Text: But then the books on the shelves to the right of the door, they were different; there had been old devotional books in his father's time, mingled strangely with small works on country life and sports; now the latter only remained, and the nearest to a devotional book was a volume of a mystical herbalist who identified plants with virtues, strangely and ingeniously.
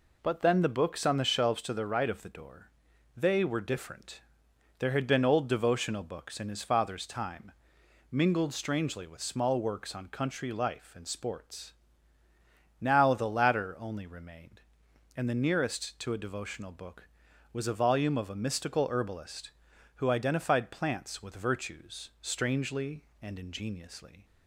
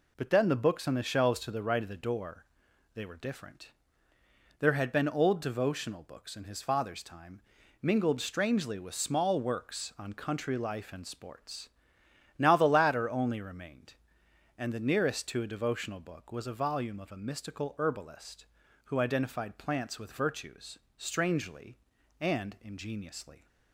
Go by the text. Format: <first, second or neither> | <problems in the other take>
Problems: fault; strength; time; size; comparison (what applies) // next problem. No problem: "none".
neither | none